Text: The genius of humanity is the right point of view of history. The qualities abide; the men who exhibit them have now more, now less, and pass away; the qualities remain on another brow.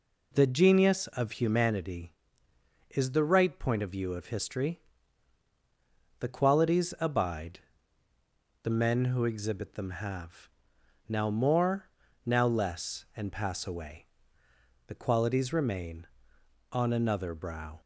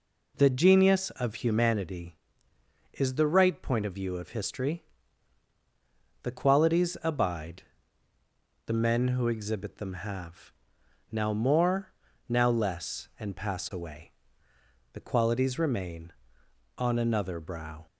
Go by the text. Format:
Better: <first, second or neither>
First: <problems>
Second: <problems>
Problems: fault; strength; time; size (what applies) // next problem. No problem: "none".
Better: neither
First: pauses between "have" and "now"; noticeable; at 10.4 s; 0.62 s long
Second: pauses between "have" and "now"; noticeable; at 10.5 s; 0.62 s long